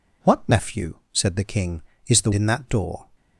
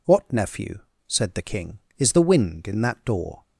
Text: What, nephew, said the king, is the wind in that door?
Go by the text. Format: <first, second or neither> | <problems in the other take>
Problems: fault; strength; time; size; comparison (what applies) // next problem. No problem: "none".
second | skips "wind"; at 2.3 s